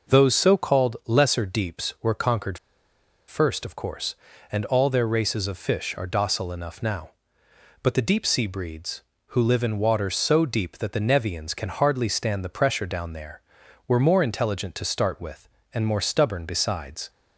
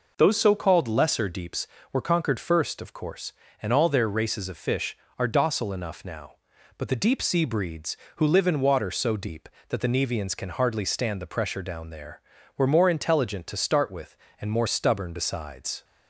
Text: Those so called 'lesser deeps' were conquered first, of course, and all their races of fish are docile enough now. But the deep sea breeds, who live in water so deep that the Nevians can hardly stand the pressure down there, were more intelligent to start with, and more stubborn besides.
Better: second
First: pauses between "conquered" and "first"; noticeable; at 2.5 s; 0.72 s long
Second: none

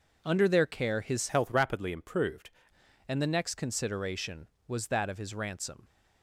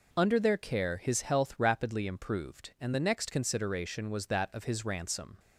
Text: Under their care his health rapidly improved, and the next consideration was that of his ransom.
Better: second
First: changes voice from "health" to "improved"; from 1.2 to 2.5 s; 1.3 s long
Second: none

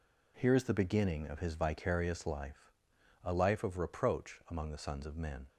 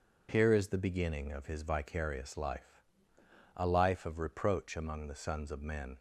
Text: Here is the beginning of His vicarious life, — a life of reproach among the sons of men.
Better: neither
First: none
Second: none

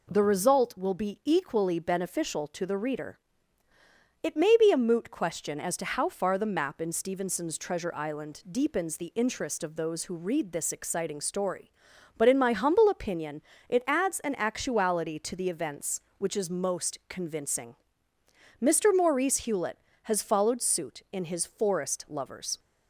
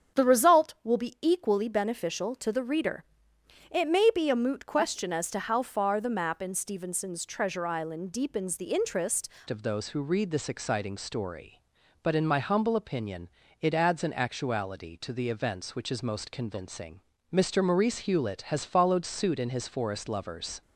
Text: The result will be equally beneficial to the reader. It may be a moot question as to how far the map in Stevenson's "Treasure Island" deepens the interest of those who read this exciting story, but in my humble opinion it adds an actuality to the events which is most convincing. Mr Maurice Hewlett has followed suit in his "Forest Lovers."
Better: first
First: pauses between "opinion" and "it"; slight; at 13.4 s; 0.26 s long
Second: starts louder than the rest; strong; until 1.2 s; 7.5 dB // changes voice at "of"; from 9.4 s on; 11.2 s long // pauses between "opinion" and "it"; slight; at 13.2 s; 0.32 s long

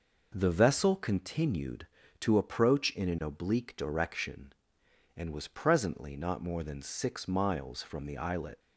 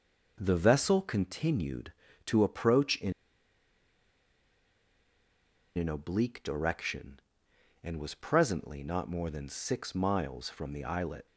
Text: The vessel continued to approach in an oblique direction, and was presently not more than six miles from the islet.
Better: first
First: none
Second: pauses between "in" and "an"; strong; at 3.1 s; 2.6 s long

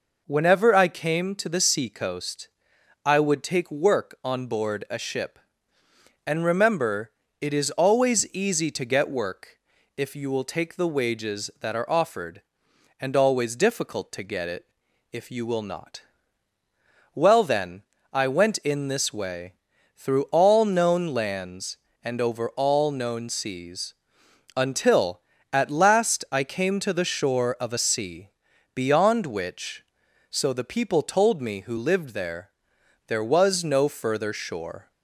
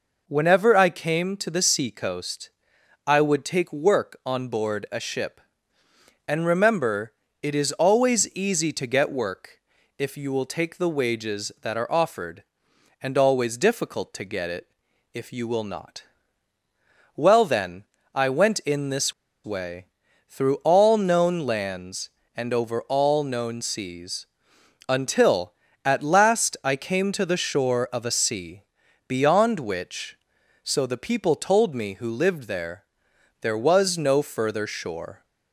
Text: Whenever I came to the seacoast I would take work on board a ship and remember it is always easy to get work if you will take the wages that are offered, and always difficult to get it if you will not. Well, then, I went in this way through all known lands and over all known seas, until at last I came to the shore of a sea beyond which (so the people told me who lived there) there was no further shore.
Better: first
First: pauses between "seacoast" and "I"; noticeable; at 2.4 s; 0.56 s long // pauses between "remember" and "it"; slight; at 7.1 s; 0.30 s long // pauses between "work" and "if"; at 9.5 s; 0.38 s long // pauses between "it" and "if"; noticeable; at 14.6 s; 0.48 s long // pauses between "way" and "through"; at 19.5 s; 0.44 s long // pauses between "sea" and "beyond"; at 28.2 s; 0.44 s long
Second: pauses between "seacoast" and "I"; noticeable; at 2.4 s; 0.56 s long // pauses between "remember" and "it"; slight; at 7.1 s; 0.30 s long // pauses between "work" and "if"; at 9.5 s; 0.38 s long // pauses between "it" and "if"; noticeable; at 14.6 s; 0.48 s long // pauses between "this" and "way"; slight; at 19.1 s; 0.31 s long // pauses between "way" and "through"; at 19.8 s; 0.44 s long // pauses between "sea" and "beyond"; at 28.6 s; 0.44 s long

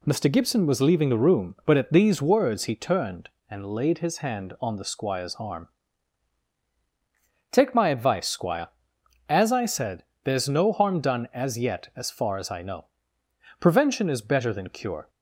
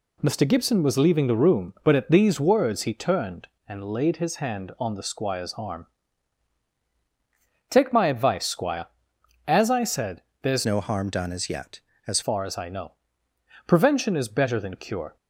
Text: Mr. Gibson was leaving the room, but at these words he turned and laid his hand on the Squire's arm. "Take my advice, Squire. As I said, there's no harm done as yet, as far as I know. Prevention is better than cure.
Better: first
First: none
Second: changes voice from "no" to "as"; from 10.6 to 12.2 s; 1.6 s long

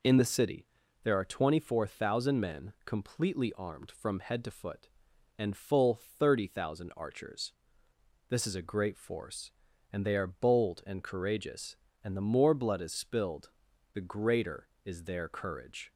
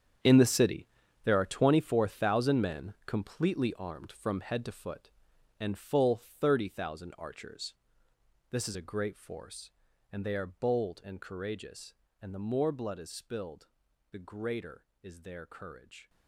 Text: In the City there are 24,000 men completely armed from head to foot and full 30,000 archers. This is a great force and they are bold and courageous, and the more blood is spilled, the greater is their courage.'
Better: first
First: pauses between "City" and "there"; slight; at 0.6 s; 0.36 s long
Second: gets quieter; strong; throughout; 13.5 dB // pauses between "City" and "there"; slight; at 0.8 s; 0.36 s long

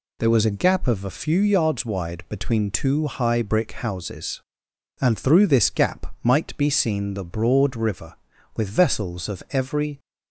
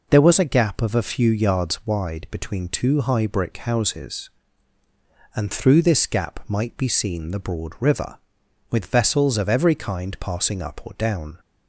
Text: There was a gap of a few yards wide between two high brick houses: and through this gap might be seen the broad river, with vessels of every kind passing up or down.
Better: second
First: stops before "kind passing up or down"; at 9.9 s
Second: none

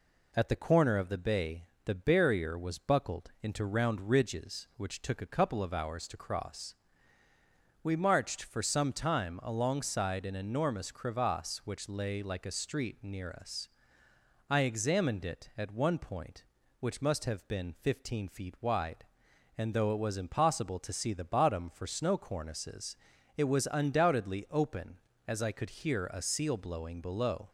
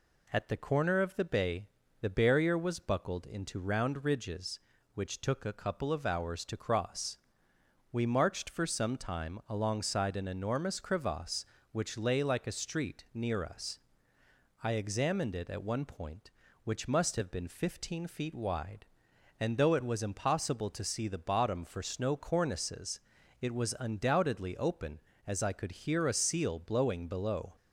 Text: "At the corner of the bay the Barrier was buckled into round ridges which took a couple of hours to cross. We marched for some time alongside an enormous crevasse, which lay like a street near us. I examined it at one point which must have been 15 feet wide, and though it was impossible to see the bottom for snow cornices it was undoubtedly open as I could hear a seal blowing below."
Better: neither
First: pauses between "bay" and "the"; slight; at 1.6 s; 0.22 s long // pauses between "cornices" and "it"; at 22.9 s; 0.42 s long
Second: pauses between "bay" and "the"; slight; at 1.6 s; 0.32 s long // pauses between "cornices" and "it"; at 23.0 s; 0.40 s long

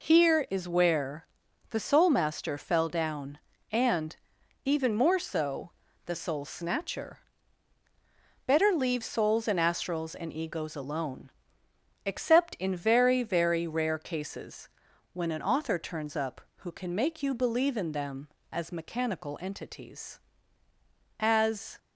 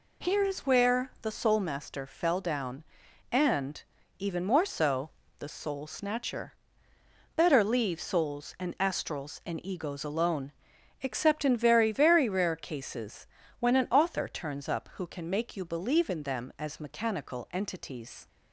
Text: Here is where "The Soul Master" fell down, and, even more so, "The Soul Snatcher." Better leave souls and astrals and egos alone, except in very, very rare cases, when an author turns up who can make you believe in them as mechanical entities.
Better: second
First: pauses between "where" and "The"; at 1.2 s; 0.42 s long // goes on to say "As"; from 21.1 s on; 0.58 s long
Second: none

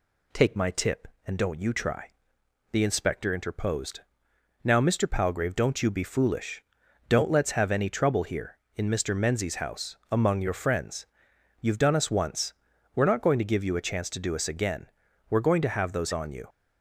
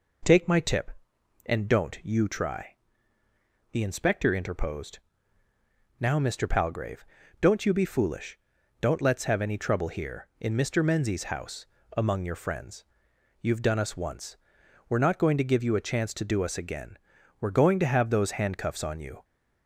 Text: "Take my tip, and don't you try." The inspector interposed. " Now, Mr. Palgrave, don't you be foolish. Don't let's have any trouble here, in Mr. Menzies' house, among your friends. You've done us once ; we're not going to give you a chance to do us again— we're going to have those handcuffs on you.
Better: second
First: skips "handcuffs"; at 16.1 s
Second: none

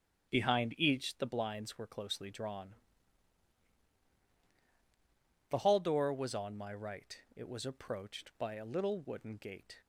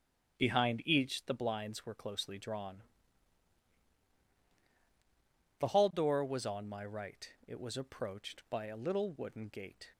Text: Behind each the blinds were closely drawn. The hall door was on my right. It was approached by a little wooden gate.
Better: neither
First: starts louder than the rest; strong; until 1.3 s; 9.5 dB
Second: starts louder than the rest; strong; until 1.4 s; 9.5 dB

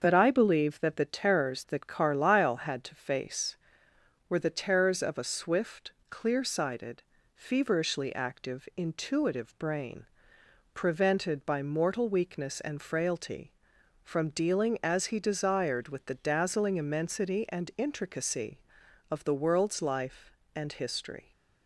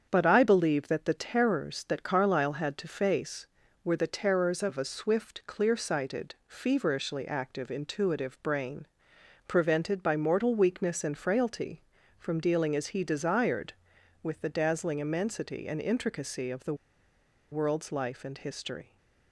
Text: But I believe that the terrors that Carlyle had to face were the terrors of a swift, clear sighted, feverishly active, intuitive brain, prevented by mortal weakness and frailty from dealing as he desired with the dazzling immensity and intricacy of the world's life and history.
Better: first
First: starts louder than the rest; until 1.0 s; 6.5 dB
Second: starts louder than the rest; strong; until 1.1 s; 7.5 dB // pauses between "the" and "world's"; noticeable; at 16.7 s; 0.77 s long

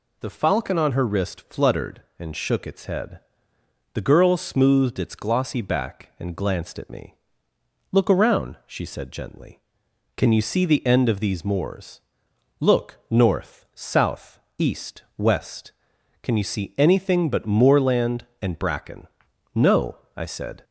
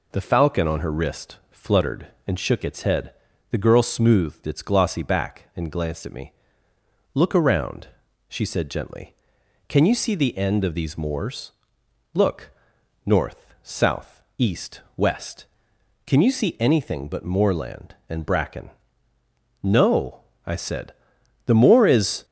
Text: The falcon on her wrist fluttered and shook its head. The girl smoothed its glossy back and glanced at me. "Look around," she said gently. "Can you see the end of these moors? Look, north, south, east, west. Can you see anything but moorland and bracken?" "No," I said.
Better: first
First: none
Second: goes on to say "The moor is"; noticeable; from 21.4 s on; 0.80 s long

